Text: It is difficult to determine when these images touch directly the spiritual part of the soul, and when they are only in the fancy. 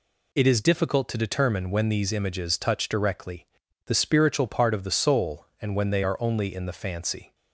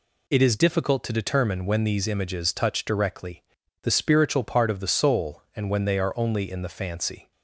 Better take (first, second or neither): neither